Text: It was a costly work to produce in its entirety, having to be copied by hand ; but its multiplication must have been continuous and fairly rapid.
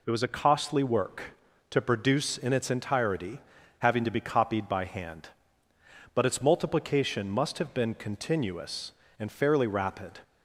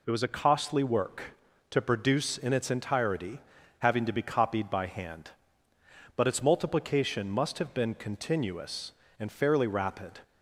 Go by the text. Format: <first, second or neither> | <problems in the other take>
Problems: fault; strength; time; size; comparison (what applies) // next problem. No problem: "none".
neither | none